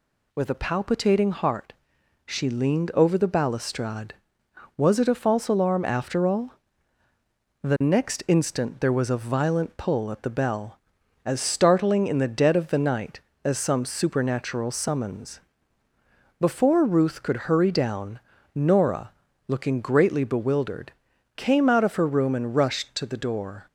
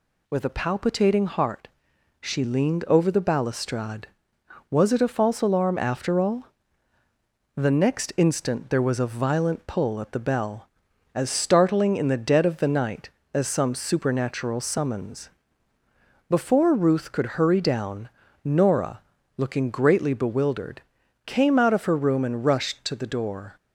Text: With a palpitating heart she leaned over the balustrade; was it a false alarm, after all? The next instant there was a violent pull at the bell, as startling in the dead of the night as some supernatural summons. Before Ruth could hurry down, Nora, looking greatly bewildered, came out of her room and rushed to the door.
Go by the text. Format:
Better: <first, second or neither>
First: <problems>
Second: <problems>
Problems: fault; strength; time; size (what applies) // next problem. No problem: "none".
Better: neither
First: pauses between "heart" and "she"; noticeable; at 1.7 s; 0.52 s long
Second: pauses between "heart" and "she"; noticeable; at 1.6 s; 0.52 s long